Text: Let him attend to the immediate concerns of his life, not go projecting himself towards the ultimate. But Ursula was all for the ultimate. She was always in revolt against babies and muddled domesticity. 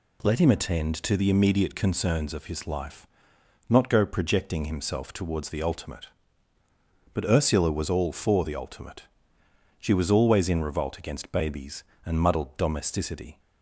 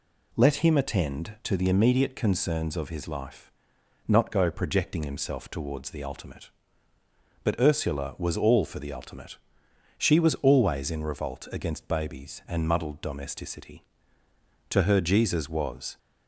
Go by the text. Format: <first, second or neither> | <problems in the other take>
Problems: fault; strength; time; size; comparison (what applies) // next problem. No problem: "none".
first | goes on to say "To her Jesus was"; noticeable; from 14.6 s on; 1.2 s long